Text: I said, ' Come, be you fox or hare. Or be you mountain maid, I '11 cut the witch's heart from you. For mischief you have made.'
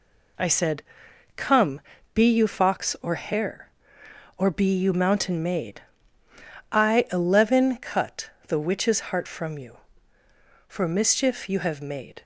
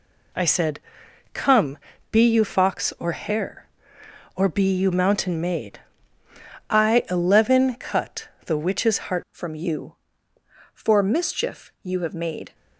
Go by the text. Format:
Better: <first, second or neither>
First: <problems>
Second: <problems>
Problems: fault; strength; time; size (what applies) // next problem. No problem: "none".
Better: first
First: pauses between "cut" and "the"; slight; at 8.3 s; 0.16 s long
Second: pauses between "cut" and "the"; slight; at 8.2 s; 0.16 s long // changes voice at "from"; from 9.3 s on; 3.2 s long